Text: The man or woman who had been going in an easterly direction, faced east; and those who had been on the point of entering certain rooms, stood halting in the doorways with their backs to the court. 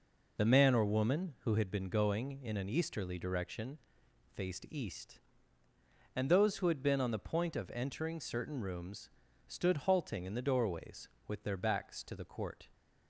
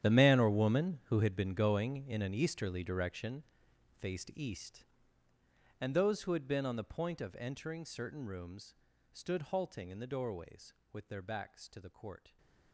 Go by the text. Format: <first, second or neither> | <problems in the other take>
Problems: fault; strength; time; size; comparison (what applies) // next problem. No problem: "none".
first | gets quieter; strong; throughout; 17 dB